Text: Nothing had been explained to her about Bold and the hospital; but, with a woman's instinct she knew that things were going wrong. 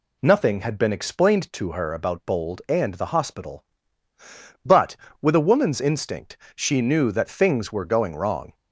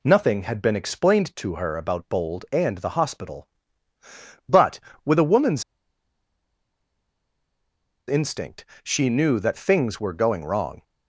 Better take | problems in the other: first | pauses between "woman's" and "instinct"; strong; at 5.6 s; 2.4 s long // pauses between "instinct" and "she"; slight; at 8.6 s; 0.18 s long; slight in the first

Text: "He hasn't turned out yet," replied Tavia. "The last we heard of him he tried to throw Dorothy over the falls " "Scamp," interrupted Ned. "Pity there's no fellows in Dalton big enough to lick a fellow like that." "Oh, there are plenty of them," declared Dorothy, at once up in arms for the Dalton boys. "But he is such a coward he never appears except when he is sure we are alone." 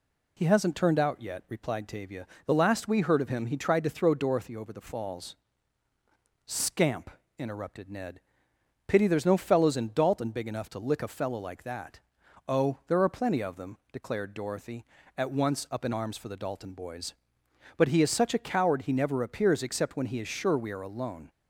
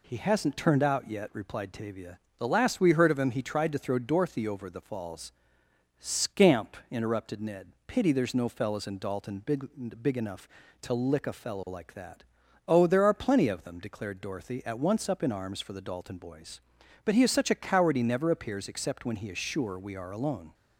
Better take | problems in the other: first | says "big" twice; at 10.0 s

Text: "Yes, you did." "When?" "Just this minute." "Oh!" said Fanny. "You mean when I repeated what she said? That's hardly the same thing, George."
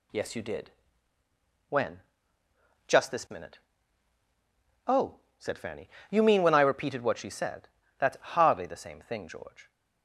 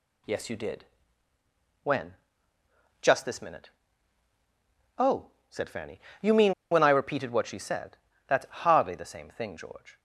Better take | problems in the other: first | pauses between "mean" and "when"; slight; at 6.5 s; 0.17 s long

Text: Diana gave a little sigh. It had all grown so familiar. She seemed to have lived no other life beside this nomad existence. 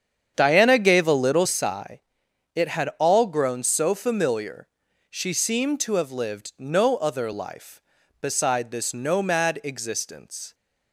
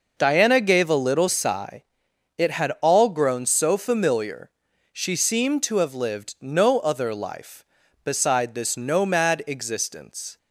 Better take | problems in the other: second | starts louder than the rest; strong; until 1.6 s; 8 dB

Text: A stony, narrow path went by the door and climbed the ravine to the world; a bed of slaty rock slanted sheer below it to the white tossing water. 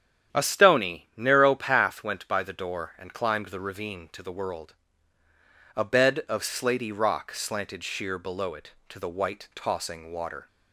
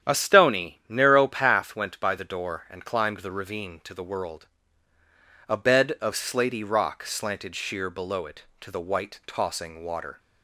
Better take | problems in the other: neither | starts louder than the rest; strong; the same in both

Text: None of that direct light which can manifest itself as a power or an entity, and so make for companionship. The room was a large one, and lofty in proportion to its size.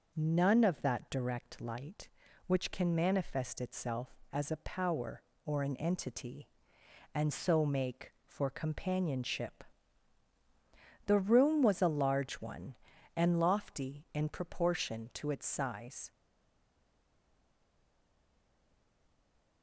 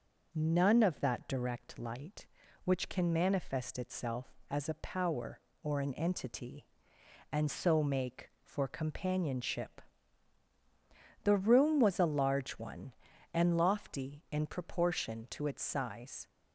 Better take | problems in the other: second | stays silent after the last word; strong; from 16.1 s on; 3.5 s long

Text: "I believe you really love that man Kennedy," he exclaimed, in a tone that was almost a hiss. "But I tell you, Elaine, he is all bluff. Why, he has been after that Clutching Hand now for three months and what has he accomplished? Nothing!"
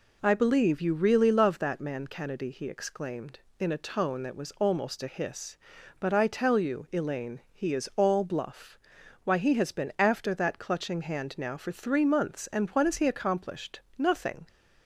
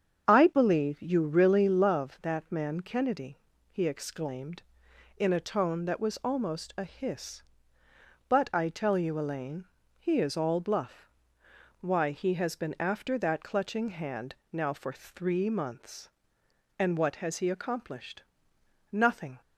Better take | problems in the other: first | starts louder than the rest; strong; until 2.0 s; 7.5 dB // pauses between "Hand" and "now"; slight; at 14.3 s; 0.16 s long

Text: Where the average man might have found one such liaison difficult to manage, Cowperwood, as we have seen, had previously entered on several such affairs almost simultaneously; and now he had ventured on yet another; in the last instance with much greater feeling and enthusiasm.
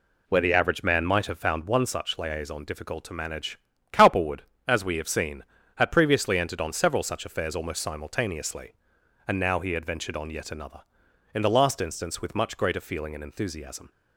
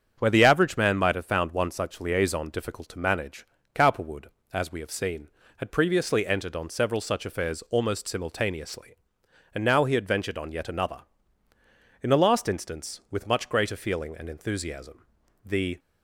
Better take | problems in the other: first | starts louder than the rest; strong; until 1.1 s; 7.5 dB // goes on to say "The"; slight; from 15.4 s on; 0.34 s long

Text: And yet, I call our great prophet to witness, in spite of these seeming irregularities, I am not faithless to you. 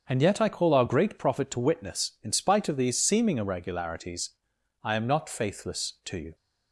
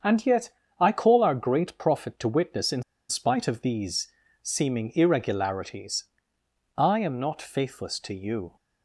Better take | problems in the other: first | starts louder than the rest; strong; until 1.3 s; 7.5 dB; also in the first // pauses between "in" and "spite"; slight; at 2.8 s; 0.26 s long // pauses between "these" and "seeming"; slight; at 4.0 s; 0.34 s long

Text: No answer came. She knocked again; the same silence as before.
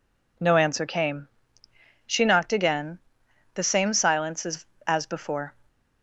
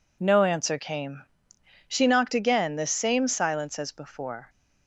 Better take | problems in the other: second | says "as" twice; at 4.8 s

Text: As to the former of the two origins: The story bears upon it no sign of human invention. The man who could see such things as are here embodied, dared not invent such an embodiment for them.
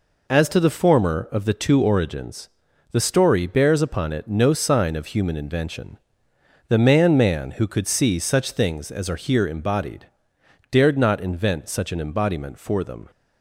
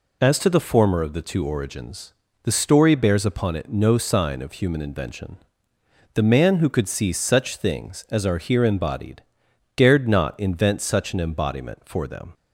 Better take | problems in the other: second | says "man" twice; at 7.1 s

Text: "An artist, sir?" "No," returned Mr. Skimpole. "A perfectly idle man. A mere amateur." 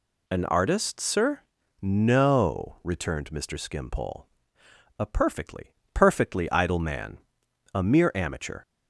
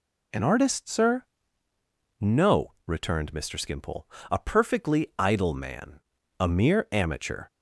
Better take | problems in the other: second | says "perfectly" twice; at 5.9 s

